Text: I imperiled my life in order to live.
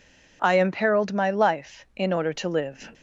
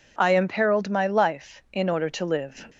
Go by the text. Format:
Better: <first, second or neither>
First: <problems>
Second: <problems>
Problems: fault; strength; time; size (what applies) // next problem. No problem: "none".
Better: neither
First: none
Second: none